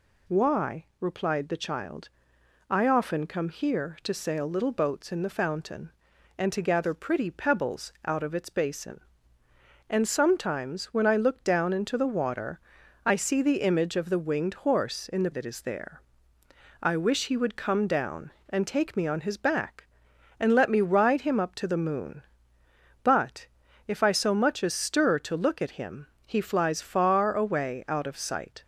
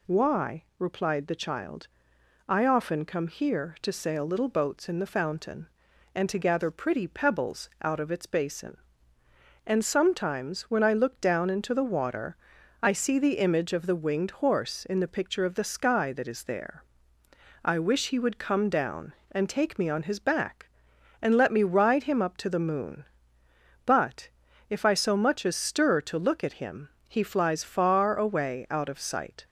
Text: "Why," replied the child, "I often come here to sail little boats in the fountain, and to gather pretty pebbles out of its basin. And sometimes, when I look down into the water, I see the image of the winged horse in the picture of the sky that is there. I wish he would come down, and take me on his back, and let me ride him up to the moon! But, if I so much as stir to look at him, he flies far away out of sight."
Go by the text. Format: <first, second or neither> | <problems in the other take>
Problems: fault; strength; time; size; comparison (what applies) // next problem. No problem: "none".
second | skips "picture of the sky"; at 15.3 s